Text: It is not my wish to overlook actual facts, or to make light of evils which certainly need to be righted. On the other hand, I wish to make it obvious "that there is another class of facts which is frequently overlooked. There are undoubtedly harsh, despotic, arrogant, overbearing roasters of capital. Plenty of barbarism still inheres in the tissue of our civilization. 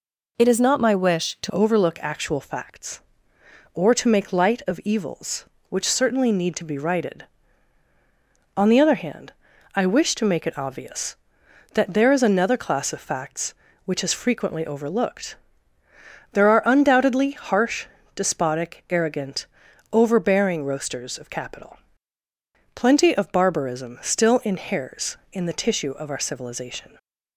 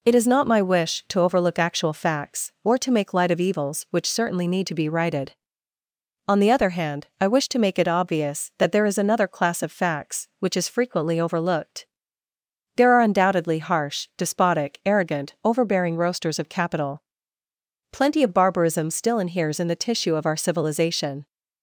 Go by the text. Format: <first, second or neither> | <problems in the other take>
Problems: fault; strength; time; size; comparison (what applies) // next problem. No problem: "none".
second | changes voice at "overlook"; from 1.5 s on; 25.4 s long